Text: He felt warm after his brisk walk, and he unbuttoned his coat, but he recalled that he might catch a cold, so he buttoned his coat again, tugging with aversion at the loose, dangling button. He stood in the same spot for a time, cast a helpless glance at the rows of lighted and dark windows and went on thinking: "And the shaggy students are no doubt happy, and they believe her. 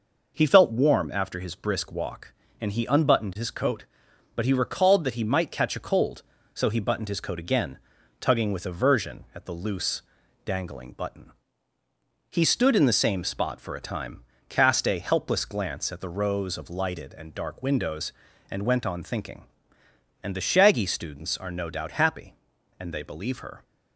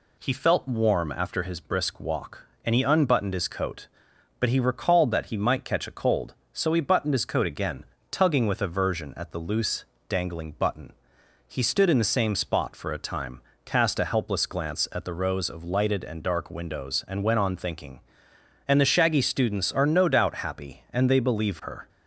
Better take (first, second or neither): neither